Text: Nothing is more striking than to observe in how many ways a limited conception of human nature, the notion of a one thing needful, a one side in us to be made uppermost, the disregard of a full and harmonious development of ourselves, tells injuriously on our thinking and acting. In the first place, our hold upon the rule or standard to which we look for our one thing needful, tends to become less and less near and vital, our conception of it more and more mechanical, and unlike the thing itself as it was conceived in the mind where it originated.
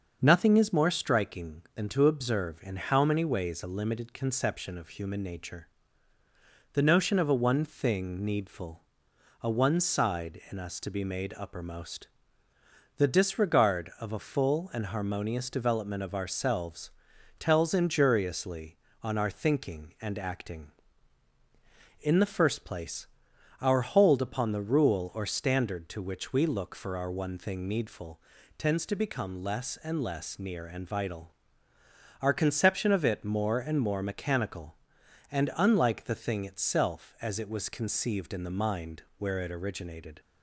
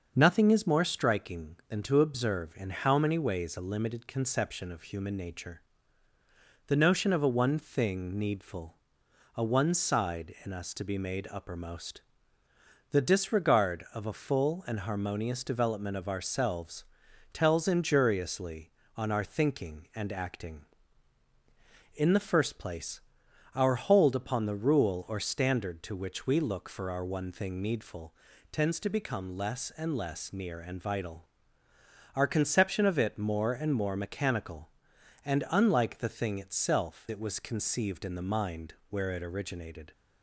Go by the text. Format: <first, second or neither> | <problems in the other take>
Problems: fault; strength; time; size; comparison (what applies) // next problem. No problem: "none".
first | starts louder than the rest; until 1.1 s; 6.5 dB; also in the first // skips "as"; at 37.0 s // pauses between "mind" and "where"; slight; at 38.7 s; 0.16 s long; slight in the first